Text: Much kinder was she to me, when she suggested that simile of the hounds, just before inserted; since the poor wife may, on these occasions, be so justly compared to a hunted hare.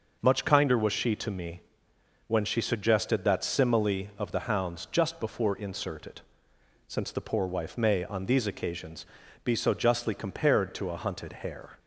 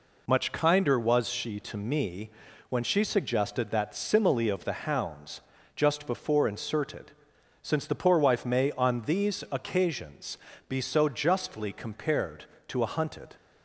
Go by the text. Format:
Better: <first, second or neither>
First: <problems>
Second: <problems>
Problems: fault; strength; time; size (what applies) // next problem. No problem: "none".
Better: first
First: none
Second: stops before "hare"; at 13.3 s